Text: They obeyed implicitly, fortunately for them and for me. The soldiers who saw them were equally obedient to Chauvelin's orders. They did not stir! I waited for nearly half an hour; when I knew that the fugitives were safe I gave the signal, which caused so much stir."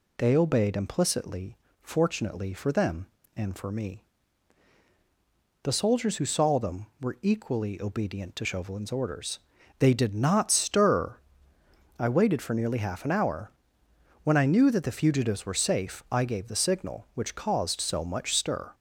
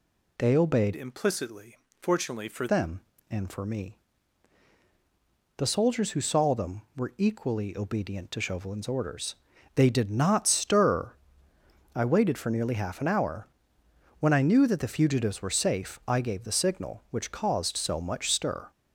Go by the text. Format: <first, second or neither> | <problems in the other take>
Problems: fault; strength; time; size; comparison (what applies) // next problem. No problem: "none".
first | changes voice from "implicitly" to "for"; from 0.9 to 2.6 s; 1.7 s long